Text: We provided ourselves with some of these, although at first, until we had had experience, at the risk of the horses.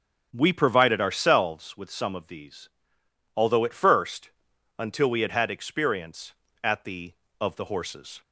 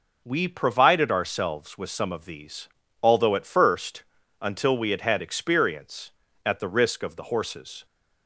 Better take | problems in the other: second | starts louder than the rest; strong; until 1.3 s; 8 dB // skips "risk"; at 7.2 s

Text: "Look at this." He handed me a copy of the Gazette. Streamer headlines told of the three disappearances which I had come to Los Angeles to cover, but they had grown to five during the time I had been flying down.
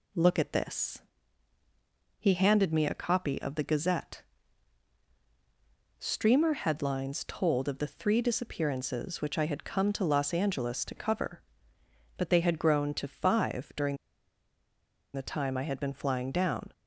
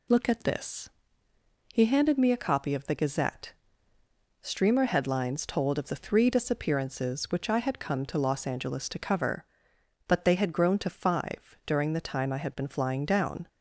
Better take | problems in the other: second | pauses between "during" and "the"; at 13.9 s; 1.1 s long

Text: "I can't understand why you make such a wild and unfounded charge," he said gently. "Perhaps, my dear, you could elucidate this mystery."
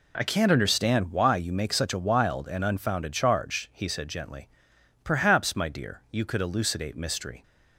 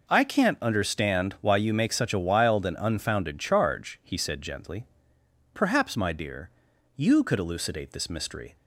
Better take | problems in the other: second | skips "this"; at 6.9 s

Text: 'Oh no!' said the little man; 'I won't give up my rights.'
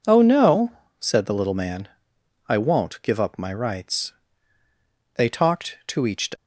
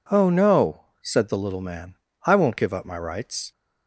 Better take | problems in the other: second | goes on to say "They talked to each"; noticeable; from 5.1 s on; 1.1 s long

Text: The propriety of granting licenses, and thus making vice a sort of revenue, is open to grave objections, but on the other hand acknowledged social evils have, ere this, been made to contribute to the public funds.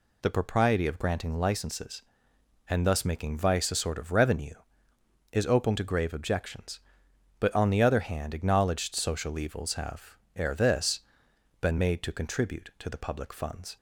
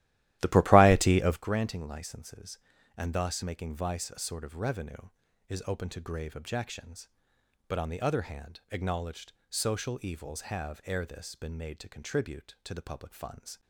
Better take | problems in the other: first | starts louder than the rest; strong; until 1.6 s; 14.5 dB // pauses between "acknowledged" and "social"; slight; at 9.3 s; 0.18 s long

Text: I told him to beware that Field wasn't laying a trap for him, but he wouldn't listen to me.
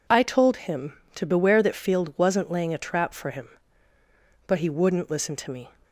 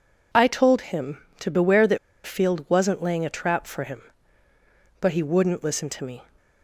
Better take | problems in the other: first | pauses between "that" and "Field"; slight; at 1.9 s; 0.27 s long

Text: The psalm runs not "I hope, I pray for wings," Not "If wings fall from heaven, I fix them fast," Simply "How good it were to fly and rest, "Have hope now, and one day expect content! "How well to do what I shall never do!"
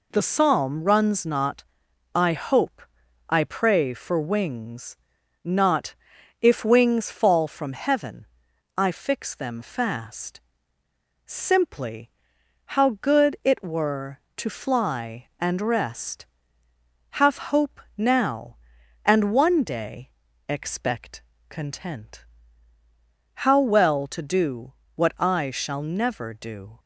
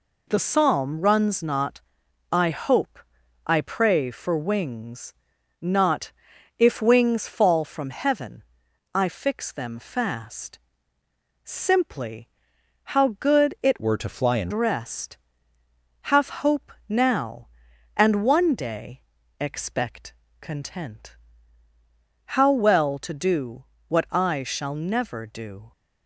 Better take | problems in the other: first | pauses between "not" and "I"; noticeable; at 1.8 s; 0.50 s long; noticeable in the first // pauses between "Not" and "If"; noticeable; at 6.1 s; 0.46 s long; noticeable in the first // pauses between "Simply" and "How"; noticeable; at 12.2 s; 0.64 s long; noticeable in the first // changes voice from "were" to "and"; from 13.8 to 14.5 s; 0.7 s long // pauses between "hope" and "now"; slight; at 16.7 s; 0.16 s long; slight in the first // pauses between "day" and "expect"; at 19.0 s; 0.38 s long; also in the first // pauses between "expect" and "content"; slight; at 20.1 s; 0.26 s long; slight in the first // pauses between "do" and "what"; slight; at 23.6 s; 0.24 s long; slight in the first

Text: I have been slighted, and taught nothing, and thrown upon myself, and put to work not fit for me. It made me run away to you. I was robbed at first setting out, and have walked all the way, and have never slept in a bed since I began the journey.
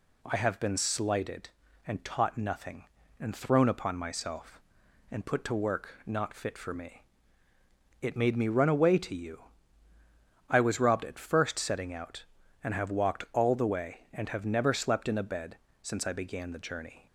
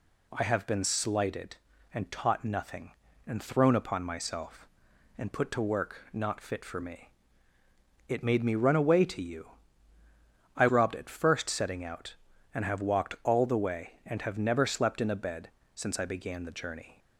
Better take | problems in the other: first | skips "was"; at 10.6 s // pauses between "bed" and "since"; slight; at 15.4 s; 0.26 s long; slight in the first

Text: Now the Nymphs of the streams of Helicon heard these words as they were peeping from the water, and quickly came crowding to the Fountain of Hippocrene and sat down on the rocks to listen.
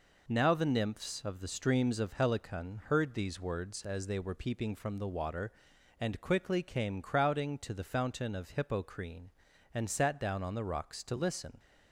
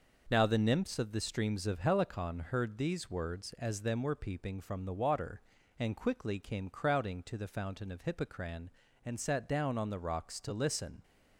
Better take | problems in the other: first | says "them" for "they"; at 3.8 s

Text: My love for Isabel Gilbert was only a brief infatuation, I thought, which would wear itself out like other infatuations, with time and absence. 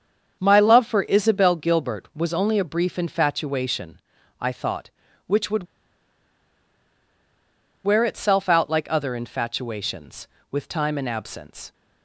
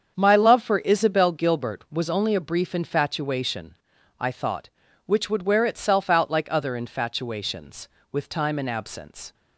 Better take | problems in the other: second | starts louder than the rest; strong; until 1.4 s; 7 dB; strong in the second // pauses between "would" and "wear"; strong; at 5.6 s; 2.1 s long

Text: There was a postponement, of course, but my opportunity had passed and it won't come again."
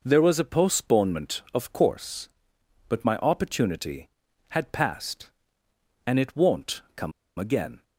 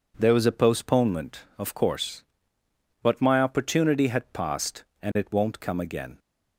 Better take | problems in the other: second | pauses between "come" and "again"; slight; at 7.1 s; 0.27 s long

